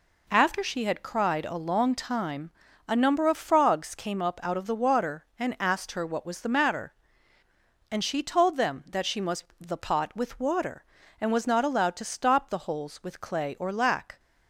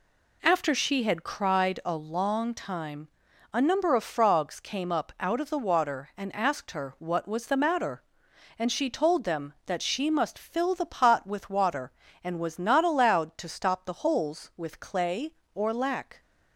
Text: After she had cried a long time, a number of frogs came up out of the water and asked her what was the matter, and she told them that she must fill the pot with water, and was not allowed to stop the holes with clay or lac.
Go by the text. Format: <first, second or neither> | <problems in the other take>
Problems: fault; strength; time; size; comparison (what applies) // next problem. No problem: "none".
second | skips "fill"; at 9.5 s